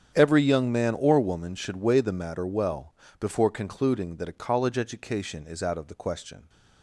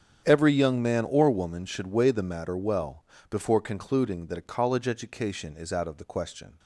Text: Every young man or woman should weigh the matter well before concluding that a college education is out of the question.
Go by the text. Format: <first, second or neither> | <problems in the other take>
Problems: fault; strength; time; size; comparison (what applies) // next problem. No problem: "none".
neither | starts louder than the rest; strong; the same in both // pauses between "well" and "before"; slight; the same in both